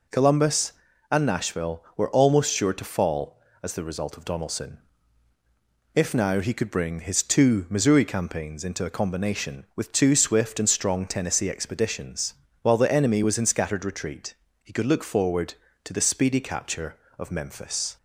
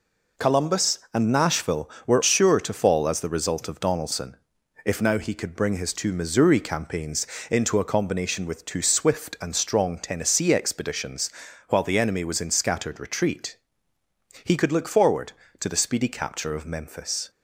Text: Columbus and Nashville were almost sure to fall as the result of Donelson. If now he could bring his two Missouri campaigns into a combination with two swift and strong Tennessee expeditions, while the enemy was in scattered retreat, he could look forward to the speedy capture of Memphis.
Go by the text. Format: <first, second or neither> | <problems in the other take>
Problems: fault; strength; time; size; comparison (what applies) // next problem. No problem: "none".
first | skips "almost"; at 2.2 s // pauses between "campaigns" and "into"; slight; at 7.2 s; 0.24 s long